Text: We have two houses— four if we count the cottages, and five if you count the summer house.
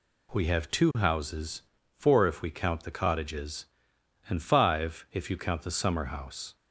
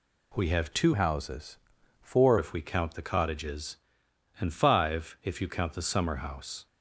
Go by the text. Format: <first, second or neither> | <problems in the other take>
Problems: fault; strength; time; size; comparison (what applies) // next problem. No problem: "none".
first | changes voice from "houses" to "four"; from 0.9 to 2.3 s; 1.4 s long